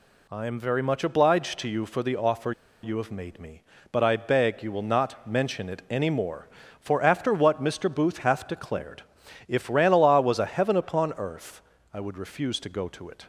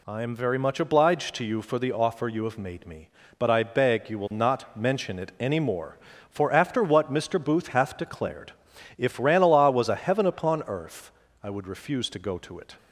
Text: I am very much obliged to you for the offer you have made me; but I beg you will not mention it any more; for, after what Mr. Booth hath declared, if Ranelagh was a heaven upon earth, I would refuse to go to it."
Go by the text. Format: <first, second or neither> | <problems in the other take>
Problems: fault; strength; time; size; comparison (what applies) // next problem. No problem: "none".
second | pauses between "offer" and "you"; slight; at 2.5 s; 0.31 s long